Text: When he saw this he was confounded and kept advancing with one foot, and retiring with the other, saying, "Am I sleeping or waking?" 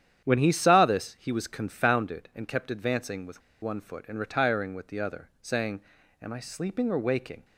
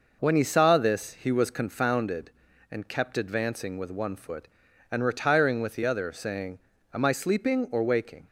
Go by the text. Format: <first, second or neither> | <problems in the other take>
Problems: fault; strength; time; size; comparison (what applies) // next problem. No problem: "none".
second | starts louder than the rest; strong; until 1.2 s; 9.5 dB // pauses between "with" and "one"; slight; at 3.4 s; 0.22 s long